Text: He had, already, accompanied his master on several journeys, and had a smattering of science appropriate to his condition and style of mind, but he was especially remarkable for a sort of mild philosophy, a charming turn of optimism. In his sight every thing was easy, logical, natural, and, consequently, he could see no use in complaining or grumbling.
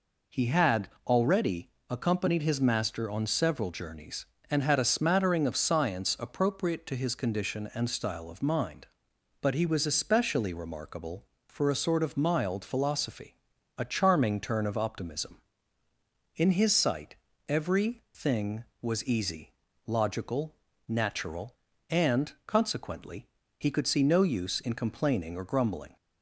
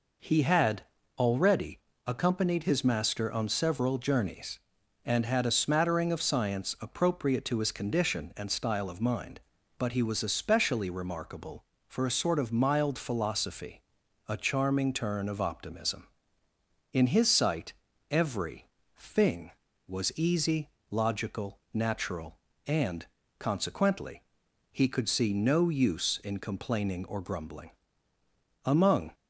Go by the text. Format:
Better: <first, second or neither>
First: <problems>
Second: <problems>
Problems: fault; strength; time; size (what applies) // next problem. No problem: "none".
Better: first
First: pauses between "sight" and "every"; slight; at 17.1 s; 0.32 s long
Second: pauses between "sight" and "every"; at 17.7 s; 0.38 s long // pauses between "every" and "thing"; slight; at 18.6 s; 0.30 s long // goes on to say "Among"; slight; from 28.6 s on; 0.48 s long